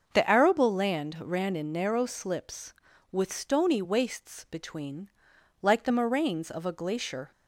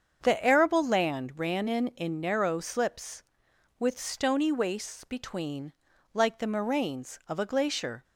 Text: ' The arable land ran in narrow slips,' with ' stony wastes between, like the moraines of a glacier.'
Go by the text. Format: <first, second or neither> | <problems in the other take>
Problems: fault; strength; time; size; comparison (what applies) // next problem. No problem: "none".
first | starts louder than the rest; strong; until 1.3 s; 7 dB; noticeable in the first // says "in" twice; at 1.9 s